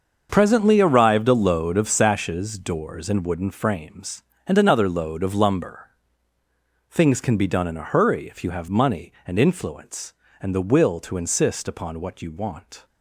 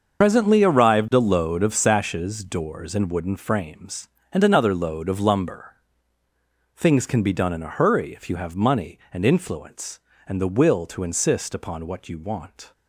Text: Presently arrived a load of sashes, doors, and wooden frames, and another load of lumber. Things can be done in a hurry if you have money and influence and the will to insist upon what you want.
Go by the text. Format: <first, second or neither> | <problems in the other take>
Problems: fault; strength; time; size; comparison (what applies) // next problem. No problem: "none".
first | loses the start of "Presently"; at 0.2 s; 80 ms // starts louder than the rest; until 1.2 s; 6.5 dB; also in the first